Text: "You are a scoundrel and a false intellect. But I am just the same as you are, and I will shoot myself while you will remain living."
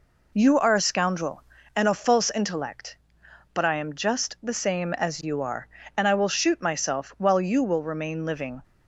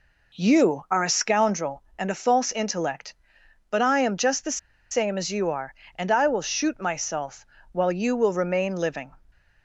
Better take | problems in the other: first | pauses between "the" and "same"; slight; at 4.5 s; 0.33 s long // pauses between "myself" and "while"; slight; at 7.4 s; 0.28 s long

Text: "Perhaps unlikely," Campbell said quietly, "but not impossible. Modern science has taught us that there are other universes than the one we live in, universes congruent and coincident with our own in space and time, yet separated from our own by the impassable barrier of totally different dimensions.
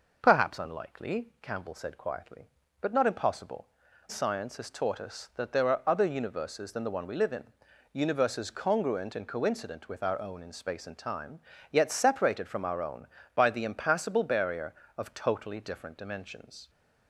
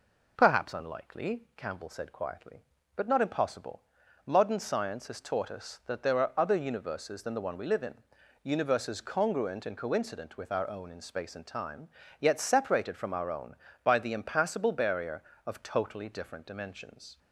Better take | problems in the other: second | skips "Modern"; at 3.8 s

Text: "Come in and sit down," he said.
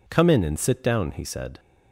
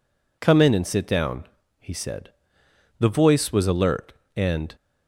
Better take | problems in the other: first | goes on to say "The voice was alert and"; strong; from 2.9 s on; 1.7 s long

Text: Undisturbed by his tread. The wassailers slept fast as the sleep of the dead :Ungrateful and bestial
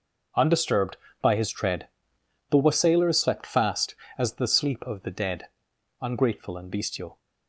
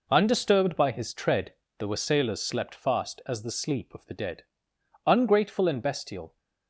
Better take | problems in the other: neither | none

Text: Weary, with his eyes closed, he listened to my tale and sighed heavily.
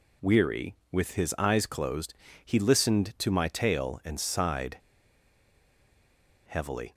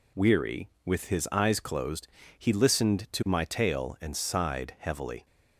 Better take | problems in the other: second | pauses between "sighed" and "heavily"; strong; at 4.7 s; 1.6 s long

